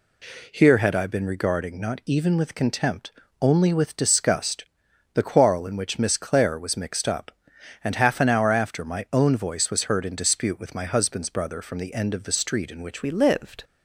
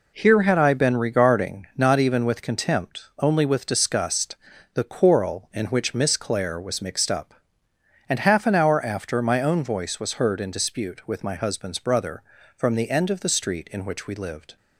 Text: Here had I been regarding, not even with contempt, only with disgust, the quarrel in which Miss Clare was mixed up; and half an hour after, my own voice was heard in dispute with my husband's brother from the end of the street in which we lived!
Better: second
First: changes voice at "we"; from 13.0 s on; 0.6 s long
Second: none

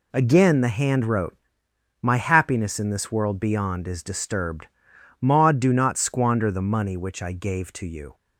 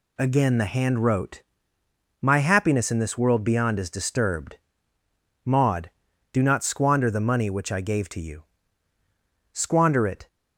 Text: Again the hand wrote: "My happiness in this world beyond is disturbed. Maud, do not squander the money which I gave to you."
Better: first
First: none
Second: goes on to say "Squander it"; noticeable; from 9.5 s on; 0.76 s long

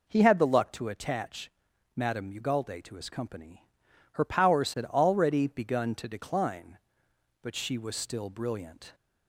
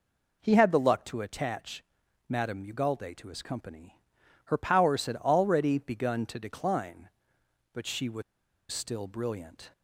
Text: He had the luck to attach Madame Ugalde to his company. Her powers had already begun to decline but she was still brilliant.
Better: first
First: pauses between "attach" and "Madame"; noticeable; at 1.5 s; 0.46 s long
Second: pauses between "attach" and "Madame"; noticeable; at 1.8 s; 0.46 s long // pauses between "was" and "still"; noticeable; at 8.2 s; 0.49 s long

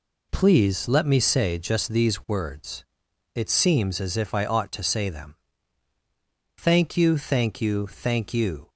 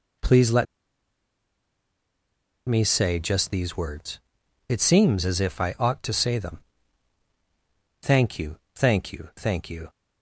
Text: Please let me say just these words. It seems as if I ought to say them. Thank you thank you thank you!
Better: first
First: none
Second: pauses between "let" and "me"; strong; at 0.6 s; 2.0 s long // pauses between "you" and "thank"; slight; at 8.5 s; 0.20 s long

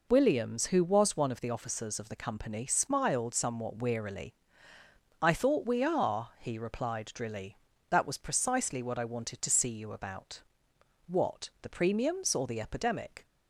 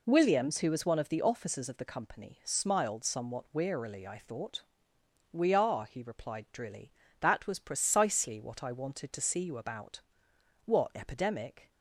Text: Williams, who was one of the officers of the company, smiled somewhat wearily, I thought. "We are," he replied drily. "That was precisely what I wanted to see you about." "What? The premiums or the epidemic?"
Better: first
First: none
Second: skips "The premiums or the"; at 10.9 s

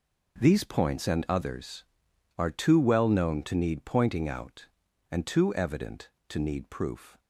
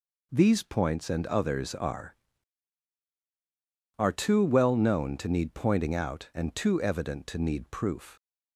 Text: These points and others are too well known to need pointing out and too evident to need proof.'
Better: first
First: none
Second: says "are" twice; at 3.9 s

